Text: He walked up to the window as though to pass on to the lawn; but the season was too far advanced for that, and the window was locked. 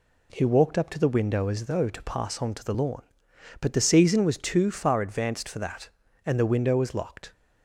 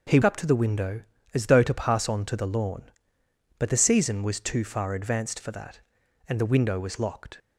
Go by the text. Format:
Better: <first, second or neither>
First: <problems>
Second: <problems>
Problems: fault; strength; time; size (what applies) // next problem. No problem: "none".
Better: first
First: none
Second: skips "walked"; at 0.2 s